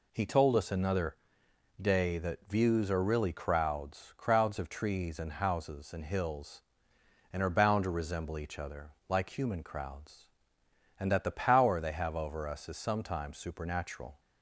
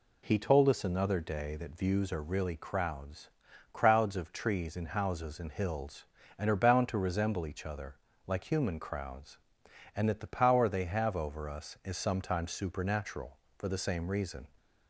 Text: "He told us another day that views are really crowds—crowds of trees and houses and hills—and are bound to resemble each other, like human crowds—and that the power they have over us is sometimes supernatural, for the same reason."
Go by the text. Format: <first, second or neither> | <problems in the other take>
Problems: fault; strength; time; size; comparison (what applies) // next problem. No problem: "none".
second | pauses between "another" and "day"; noticeable; at 1.1 s; 0.64 s long // stops before "for the same reason"; at 14.1 s